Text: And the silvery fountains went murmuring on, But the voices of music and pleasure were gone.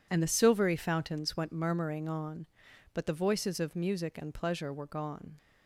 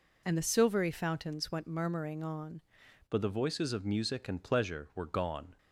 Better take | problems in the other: first | changes voice at "But"; from 3.0 s on; 2.5 s long

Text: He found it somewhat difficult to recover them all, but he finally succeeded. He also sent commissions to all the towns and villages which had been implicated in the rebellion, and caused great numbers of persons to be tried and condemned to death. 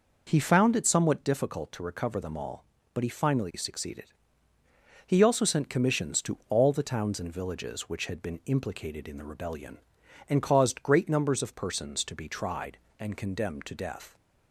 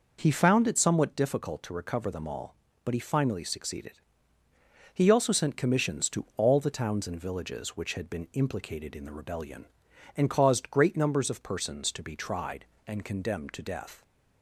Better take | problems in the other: neither | none

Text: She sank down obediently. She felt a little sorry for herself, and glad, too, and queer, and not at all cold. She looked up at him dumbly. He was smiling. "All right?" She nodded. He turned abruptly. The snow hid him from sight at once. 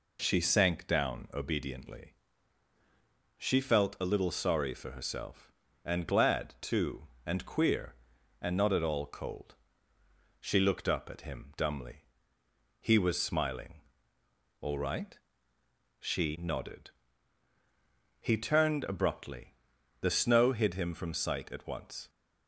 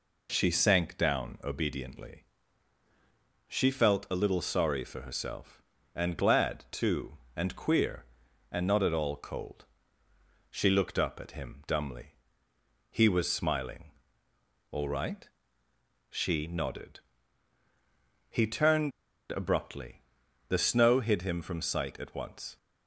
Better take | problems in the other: first | pauses between "turned" and "abruptly"; at 18.9 s; 0.39 s long

